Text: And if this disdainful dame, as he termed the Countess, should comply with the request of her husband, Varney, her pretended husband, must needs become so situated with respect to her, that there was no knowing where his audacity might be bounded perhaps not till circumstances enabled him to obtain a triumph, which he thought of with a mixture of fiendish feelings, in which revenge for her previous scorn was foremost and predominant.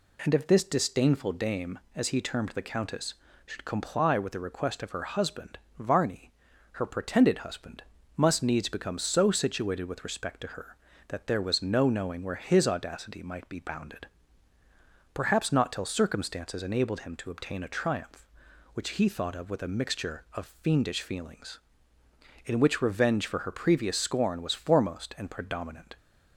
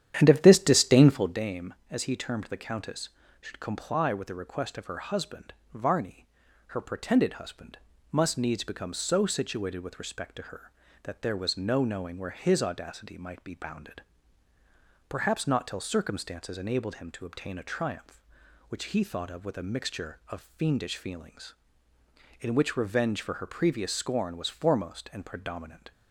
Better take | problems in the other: first | starts louder than the rest; strong; until 1.4 s; 10.5 dB // pauses between "bounded" and "perhaps"; at 14.0 s; 1.0 s long; also in the first

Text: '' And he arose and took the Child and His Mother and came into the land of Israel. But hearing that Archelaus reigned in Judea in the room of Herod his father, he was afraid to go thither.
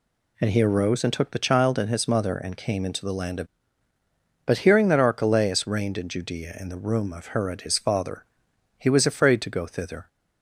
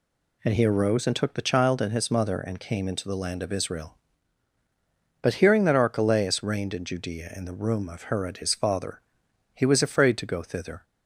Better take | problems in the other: second | skips "Israel"; at 3.9 s

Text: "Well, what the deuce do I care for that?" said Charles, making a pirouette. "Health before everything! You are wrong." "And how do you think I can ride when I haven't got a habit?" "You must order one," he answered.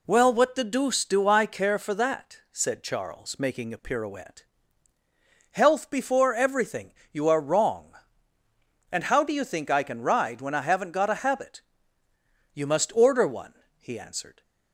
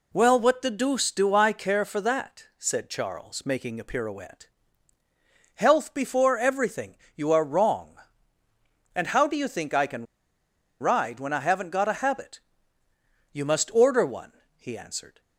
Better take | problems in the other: first | pauses between "can" and "ride"; noticeable; at 10.0 s; 0.77 s long

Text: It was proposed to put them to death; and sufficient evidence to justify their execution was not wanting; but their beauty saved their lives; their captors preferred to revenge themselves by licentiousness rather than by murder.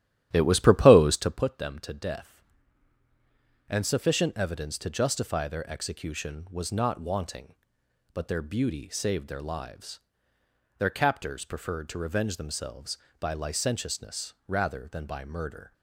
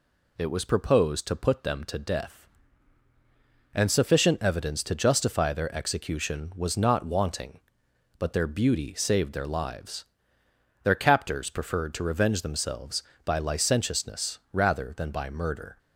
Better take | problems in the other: second | starts louder than the rest; strong; until 1.4 s; 11.5 dB

